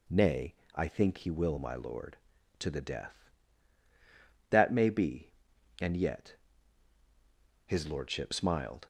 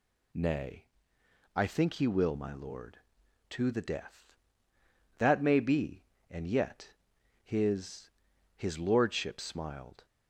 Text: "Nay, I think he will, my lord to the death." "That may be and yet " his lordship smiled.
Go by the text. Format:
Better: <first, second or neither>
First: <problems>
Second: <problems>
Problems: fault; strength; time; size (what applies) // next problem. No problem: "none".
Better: first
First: none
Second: says "his" twice; at 8.5 s